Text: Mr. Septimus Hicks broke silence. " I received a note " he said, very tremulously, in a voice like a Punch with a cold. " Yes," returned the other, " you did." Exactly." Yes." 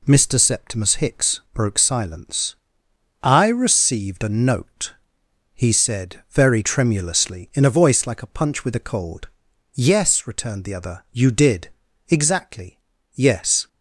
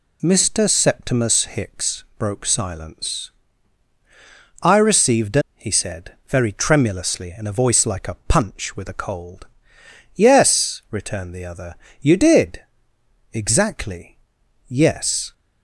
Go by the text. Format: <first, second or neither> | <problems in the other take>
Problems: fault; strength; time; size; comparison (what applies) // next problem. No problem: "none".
first | skips "note"; at 5.4 s